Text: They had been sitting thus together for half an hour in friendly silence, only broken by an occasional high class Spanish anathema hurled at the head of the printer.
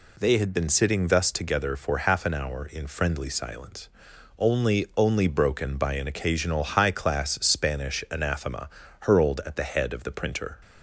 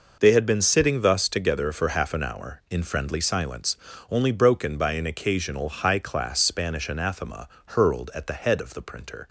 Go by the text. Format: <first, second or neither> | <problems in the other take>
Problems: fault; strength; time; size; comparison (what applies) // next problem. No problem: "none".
second | says "only" twice; at 4.9 s // pauses between "anathema" and "hurled"; slight; at 8.6 s; 0.32 s long; slight in the second